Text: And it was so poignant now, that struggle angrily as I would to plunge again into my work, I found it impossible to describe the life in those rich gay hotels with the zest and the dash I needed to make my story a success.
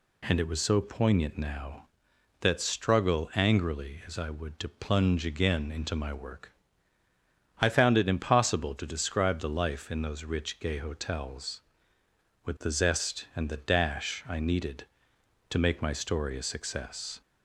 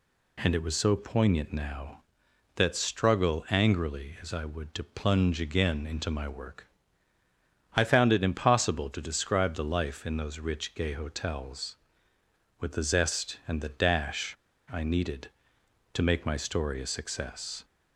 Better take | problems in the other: first | pauses between "dash" and "I"; at 14.3 s; 0.38 s long

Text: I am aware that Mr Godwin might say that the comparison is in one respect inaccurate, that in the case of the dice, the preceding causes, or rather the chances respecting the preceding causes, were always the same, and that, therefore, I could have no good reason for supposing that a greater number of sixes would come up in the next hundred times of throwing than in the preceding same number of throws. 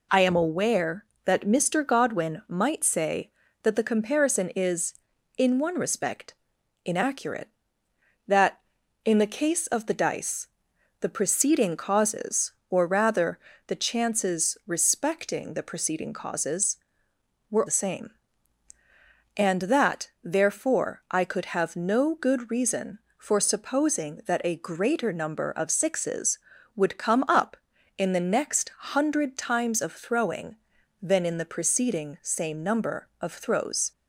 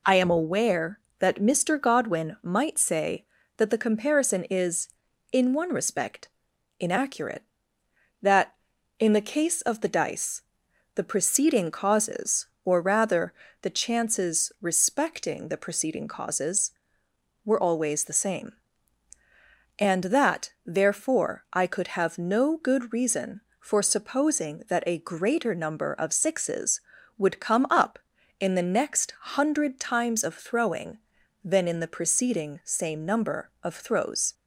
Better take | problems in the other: second | pauses between "respect" and "inaccurate"; noticeable; at 6.3 s; 0.52 s long; noticeable in the second // pauses between "rather" and "the"; slight; at 13.3 s; 0.28 s long; slight in the second // skips "always"; at 17.6 s

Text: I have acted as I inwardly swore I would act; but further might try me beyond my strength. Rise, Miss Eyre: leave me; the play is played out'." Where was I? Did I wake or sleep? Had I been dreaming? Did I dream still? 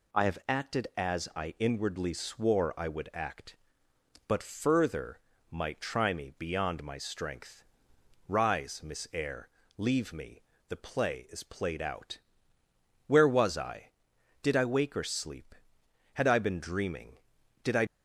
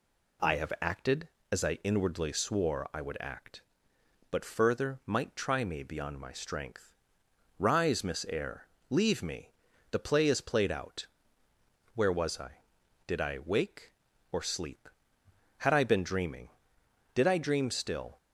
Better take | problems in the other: second | pauses between "further" and "might"; slight; at 5.2 s; 0.30 s long // stops before "dream still"; at 17.8 s

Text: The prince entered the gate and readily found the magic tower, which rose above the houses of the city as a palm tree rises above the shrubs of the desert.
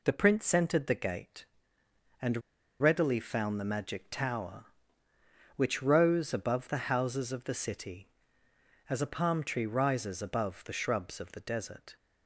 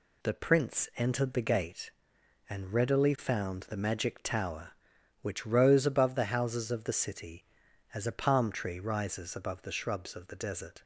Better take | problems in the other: second | pauses between "and" and "readily"; at 2.4 s; 0.38 s long

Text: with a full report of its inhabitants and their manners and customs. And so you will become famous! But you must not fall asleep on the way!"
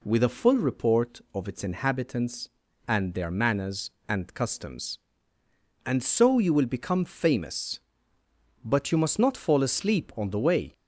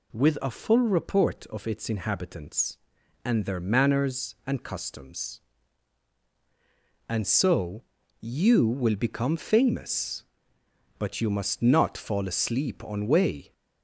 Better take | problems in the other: first | pauses between "so" and "you"; at 7.8 s; 0.38 s long // skips "the"; at 13.0 s

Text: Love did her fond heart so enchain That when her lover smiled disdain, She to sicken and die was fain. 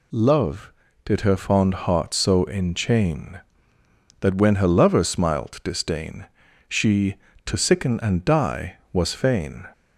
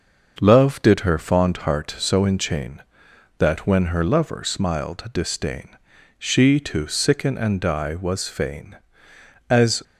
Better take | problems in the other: first | starts louder than the rest; noticeable; until 1.4 s; 6 dB // goes on to say "As"; slight; from 9.4 s on; 0.34 s long

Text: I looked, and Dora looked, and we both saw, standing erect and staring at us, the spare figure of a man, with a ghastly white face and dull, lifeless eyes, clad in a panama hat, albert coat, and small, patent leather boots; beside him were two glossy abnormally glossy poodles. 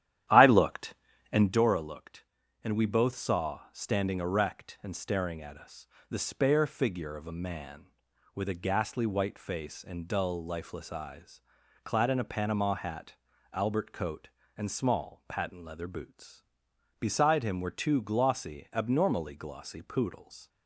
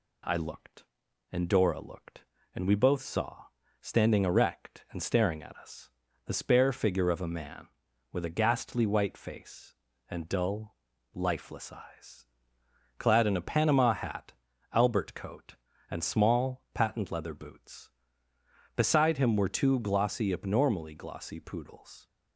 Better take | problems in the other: second | starts louder than the rest; strong; until 1.6 s; 11.5 dB

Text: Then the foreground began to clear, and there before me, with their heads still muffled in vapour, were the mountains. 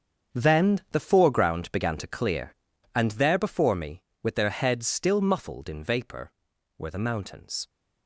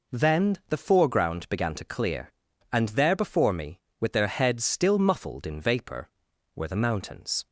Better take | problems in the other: second | gets quieter; strong; throughout; 12 dB

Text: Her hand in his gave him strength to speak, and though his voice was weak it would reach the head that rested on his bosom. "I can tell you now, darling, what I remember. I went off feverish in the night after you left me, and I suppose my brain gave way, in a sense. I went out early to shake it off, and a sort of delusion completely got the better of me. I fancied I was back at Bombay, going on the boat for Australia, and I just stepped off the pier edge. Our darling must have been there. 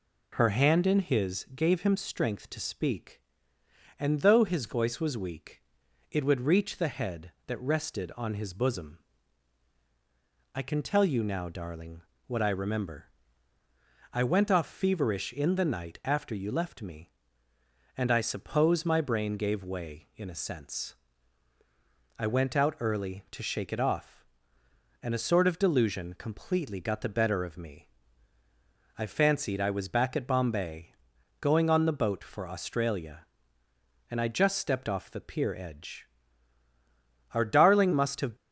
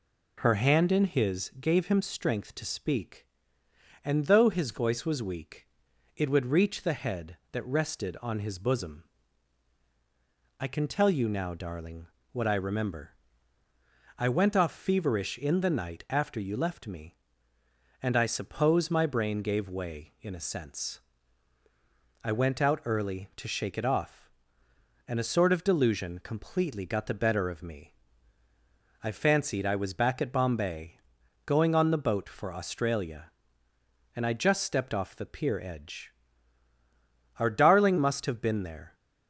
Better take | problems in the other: second | pauses between "weak" and "it"; noticeable; at 5.6 s; 0.48 s long; noticeable in the second // stops before "been there"; at 38.3 s

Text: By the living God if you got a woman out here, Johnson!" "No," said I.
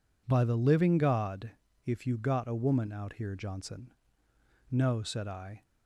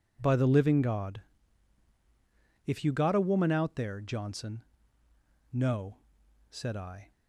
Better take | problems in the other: first | pauses between "God" and "if"; strong; at 1.2 s; 1.4 s long; slight in the first // says "there" for "here"; at 3.7 s

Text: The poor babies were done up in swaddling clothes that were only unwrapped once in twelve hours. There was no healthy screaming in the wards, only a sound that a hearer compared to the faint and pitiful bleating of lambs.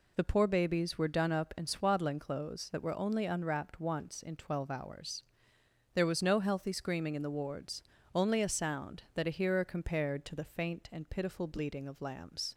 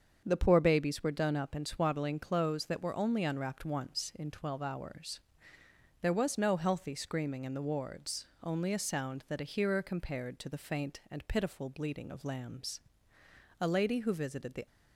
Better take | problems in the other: first | starts louder than the rest; until 1.2 s; 7 dB // goes on to say "A lady who visited the"; noticeable; from 13.5 s on; 1.0 s long

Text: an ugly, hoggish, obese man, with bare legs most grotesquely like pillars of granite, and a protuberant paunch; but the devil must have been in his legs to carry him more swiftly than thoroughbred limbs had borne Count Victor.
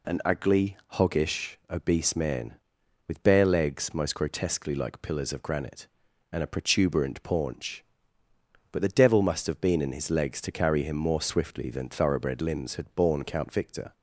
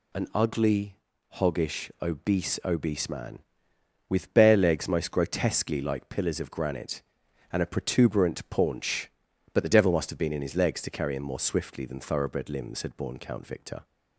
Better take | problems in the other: first | says "obese" twice; at 2.6 s

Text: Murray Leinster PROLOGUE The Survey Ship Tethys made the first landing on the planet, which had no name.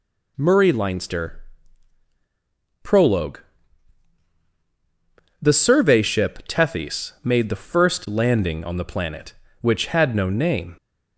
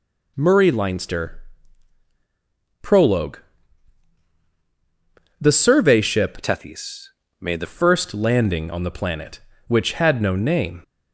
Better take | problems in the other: first | pauses between "Leinster" and "PROLOGUE"; strong; at 1.4 s; 1.3 s long; strong in the first // pauses between "PROLOGUE" and "The"; strong; at 3.3 s; 2.0 s long; strong in the first // changes voice from "Tethys" to "the"; from 6.4 to 7.6 s; 1.2 s long // pauses between "Tethys" and "made"; slight; at 7.0 s; 0.30 s long

